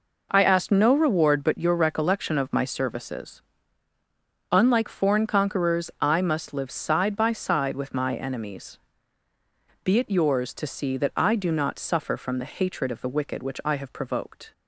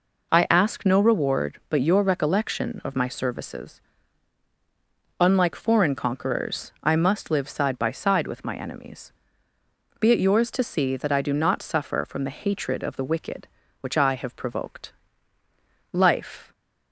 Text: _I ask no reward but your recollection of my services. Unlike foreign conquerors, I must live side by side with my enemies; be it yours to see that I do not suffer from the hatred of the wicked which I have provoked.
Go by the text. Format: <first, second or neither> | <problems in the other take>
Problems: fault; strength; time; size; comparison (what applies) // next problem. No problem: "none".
first | goes on to say "Life"; from 15.9 s on; 0.60 s long